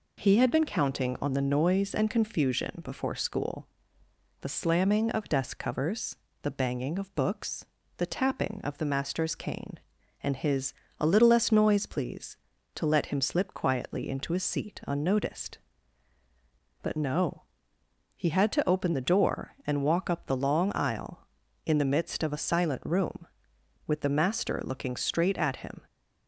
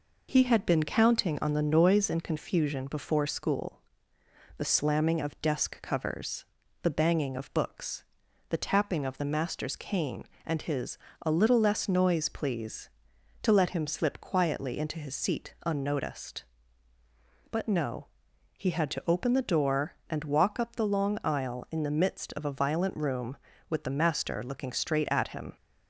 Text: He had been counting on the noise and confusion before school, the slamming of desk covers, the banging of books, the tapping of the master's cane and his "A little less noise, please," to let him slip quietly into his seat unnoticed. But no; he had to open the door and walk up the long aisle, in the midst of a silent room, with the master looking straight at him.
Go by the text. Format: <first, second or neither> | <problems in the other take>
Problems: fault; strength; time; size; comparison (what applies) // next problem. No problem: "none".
first | pauses between "his" and "A"; slight; at 10.9 s; 0.24 s long; slight in the first // says "violent" for "silent"; at 22.5 s